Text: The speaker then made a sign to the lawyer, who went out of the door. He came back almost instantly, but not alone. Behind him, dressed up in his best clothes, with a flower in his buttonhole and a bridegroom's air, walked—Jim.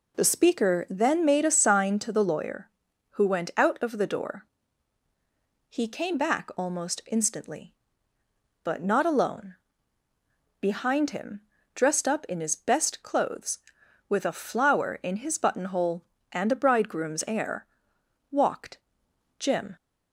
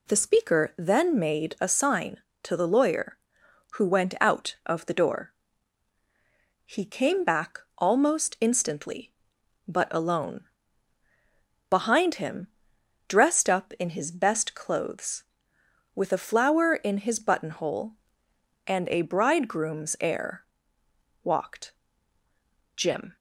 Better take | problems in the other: first | pauses between "back" and "almost"; slight; at 7.5 s; 0.18 s long // skips "not"; at 9.8 s

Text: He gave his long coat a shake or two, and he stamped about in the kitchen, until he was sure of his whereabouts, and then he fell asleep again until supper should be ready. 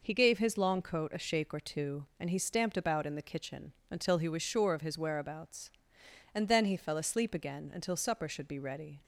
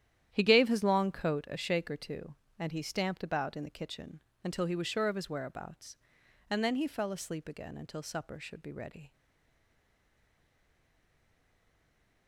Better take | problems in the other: first | starts louder than the rest; strong; until 1.3 s; 11 dB // stays silent after the last word; strong; from 9.1 s on; 3.1 s long

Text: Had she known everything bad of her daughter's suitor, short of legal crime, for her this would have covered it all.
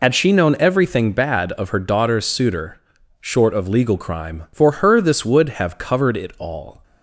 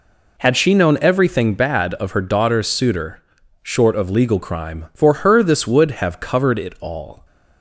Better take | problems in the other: second | loses the start of "Had"; at 0.0 s; 50 ms

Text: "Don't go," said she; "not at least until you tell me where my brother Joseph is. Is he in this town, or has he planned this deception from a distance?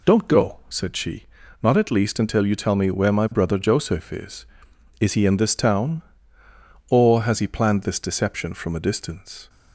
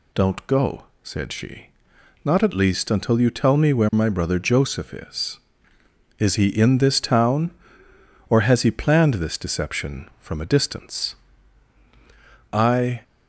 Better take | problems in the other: first | goes on to say "I"; from 12.5 s on; 0.50 s long

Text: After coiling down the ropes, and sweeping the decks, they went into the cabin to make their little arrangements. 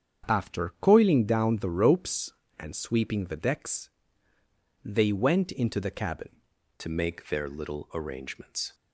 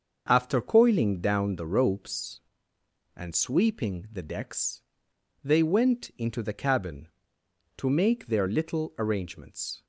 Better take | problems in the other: second | starts louder than the rest; strong; until 1.3 s; 8 dB; also in the second // changes voice at "to"; from 6.7 s on; 2.0 s long

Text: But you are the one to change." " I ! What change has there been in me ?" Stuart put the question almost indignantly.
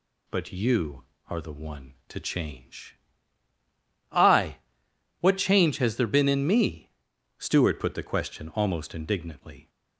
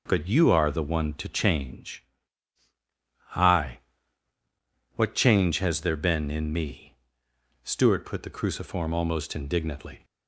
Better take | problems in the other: first | says "cruciform" for "question"; at 8.3 s

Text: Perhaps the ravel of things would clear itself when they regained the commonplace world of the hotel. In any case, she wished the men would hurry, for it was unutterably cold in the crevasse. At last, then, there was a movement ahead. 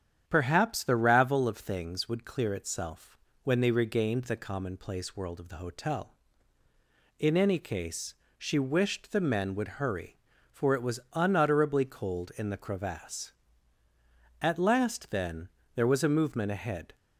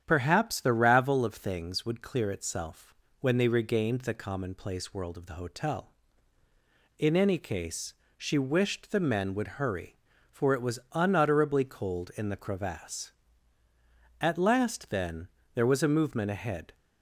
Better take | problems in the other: neither | starts louder than the rest; strong; the same in both // pauses between "itself" and "when"; slight; the same in both

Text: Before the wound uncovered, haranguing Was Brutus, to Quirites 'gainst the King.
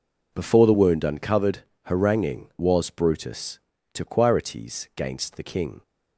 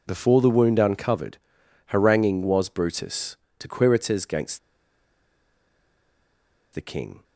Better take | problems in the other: first | pauses between "gainst" and "the"; strong; at 4.5 s; 2.1 s long

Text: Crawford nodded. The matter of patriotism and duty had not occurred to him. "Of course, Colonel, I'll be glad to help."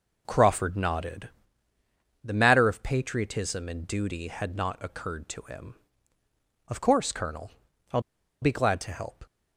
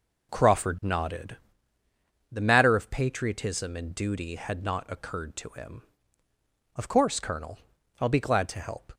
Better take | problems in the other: second | pauses between "I'll" and "be"; at 8.0 s; 0.41 s long

